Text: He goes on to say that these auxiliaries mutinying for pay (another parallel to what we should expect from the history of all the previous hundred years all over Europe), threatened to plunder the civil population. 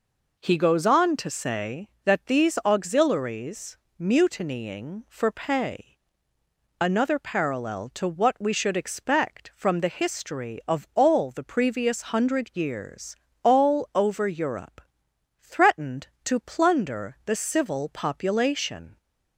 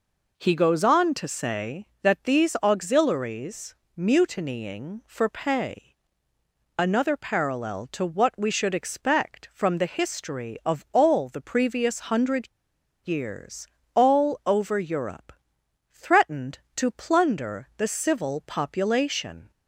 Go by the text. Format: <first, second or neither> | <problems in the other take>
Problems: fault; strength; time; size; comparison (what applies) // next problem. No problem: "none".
first | pauses between "auxiliaries" and "mutinying"; slight; at 3.7 s; 0.20 s long; slight in the first // pauses between "hundred" and "years"; noticeable; at 12.4 s; 0.55 s long // pauses between "years" and "all"; slight; at 13.6 s; 0.26 s long; slight in the first